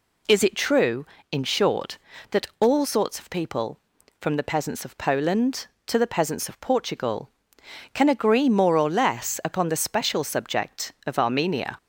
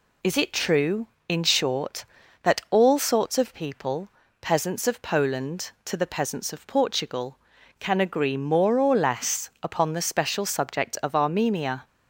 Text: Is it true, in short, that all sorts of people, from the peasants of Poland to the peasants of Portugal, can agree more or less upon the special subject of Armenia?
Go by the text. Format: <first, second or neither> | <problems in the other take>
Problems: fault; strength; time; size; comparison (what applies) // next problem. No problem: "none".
first | skips "from the"; at 4.2 s